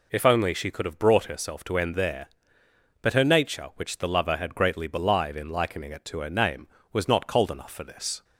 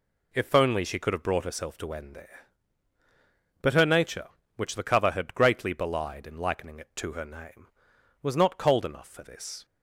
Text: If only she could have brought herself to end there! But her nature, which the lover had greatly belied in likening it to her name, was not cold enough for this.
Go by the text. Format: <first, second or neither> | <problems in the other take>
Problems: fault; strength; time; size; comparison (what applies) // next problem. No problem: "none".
first | says "cover" for "lover"; at 4.8 s